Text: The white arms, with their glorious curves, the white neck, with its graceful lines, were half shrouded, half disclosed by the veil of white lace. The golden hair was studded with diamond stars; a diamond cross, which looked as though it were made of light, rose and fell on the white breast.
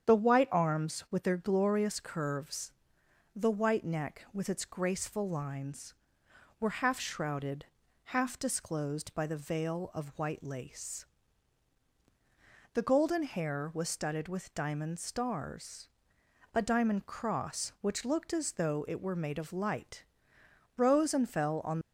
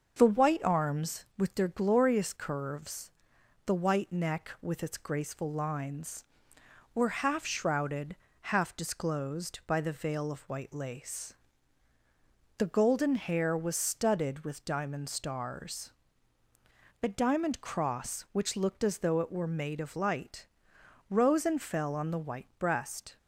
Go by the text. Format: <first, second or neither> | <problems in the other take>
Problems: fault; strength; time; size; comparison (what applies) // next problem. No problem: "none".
second | starts louder than the rest; strong; until 1.1 s; 8.5 dB; also in the second // stops before "the white breast"; at 21.8 s